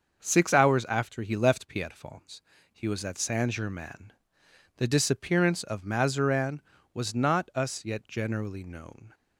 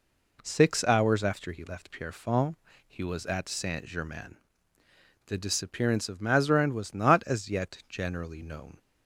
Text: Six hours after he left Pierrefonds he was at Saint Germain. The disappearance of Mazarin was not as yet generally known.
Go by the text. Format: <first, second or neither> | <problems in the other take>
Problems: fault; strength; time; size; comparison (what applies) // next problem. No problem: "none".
second | starts louder than the rest; until 1.2 s; 6.5 dB // pauses between "Pierrefonds" and "he"; slight; at 2.4 s; 0.32 s long; slight in the second // says "us" for "as"; at 7.5 s